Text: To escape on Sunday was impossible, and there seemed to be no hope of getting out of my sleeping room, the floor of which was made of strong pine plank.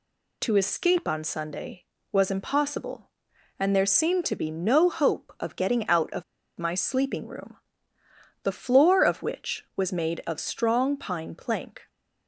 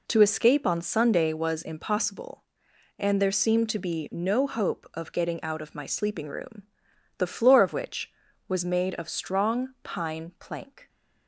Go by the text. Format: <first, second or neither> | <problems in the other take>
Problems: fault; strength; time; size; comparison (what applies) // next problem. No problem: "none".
second | pauses between "of" and "my"; slight; at 6.2 s; 0.35 s long